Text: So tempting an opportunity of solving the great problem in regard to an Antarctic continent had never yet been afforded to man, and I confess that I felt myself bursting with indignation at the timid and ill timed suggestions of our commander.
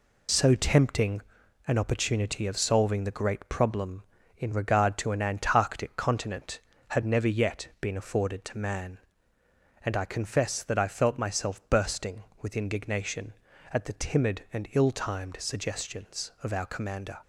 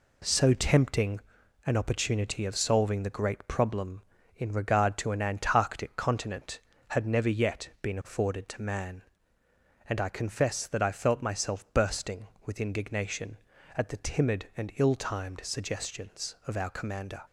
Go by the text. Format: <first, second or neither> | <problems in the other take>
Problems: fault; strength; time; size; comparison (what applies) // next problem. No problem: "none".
second | loses the start of "So"; at 0.2 s; 55 ms // pauses between "tempting" and "an"; noticeable; at 1.2 s; 0.48 s long; noticeable in the second